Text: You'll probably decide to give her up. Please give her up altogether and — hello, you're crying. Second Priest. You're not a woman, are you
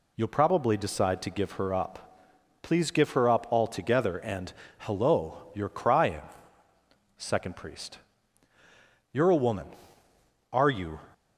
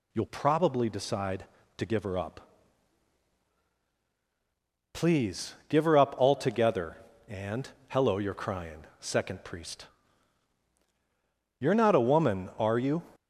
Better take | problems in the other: second | skips "not"; at 9.2 s

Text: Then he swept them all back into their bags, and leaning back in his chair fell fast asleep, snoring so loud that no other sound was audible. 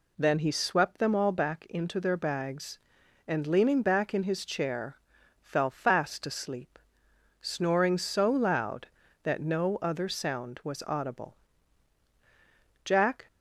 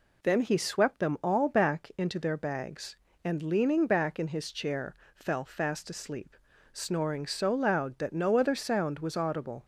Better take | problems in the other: second | pauses between "chair" and "fell"; noticeable; at 4.9 s; 0.46 s long; slight in the second // goes on to say "Jack"; slight; from 12.8 s on; 0.42 s long

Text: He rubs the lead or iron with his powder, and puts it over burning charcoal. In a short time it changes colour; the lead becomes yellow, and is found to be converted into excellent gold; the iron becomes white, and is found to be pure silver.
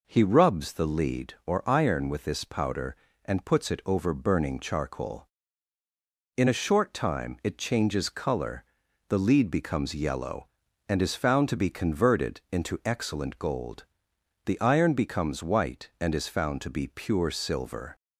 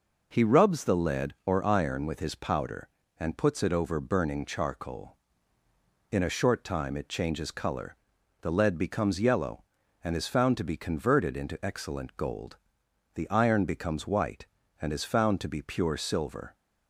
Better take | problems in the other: second | says "this" for "his"; at 2.2 s

